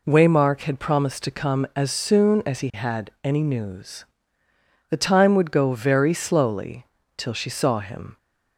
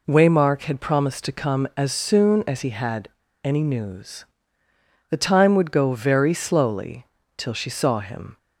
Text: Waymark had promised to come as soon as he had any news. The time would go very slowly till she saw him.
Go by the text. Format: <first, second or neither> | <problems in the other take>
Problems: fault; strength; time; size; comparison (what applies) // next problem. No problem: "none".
first | pauses between "had" and "any"; at 3.0 s; 0.36 s long // pauses between "slowly" and "till"; slight; at 7.0 s; 0.32 s long; slight in the first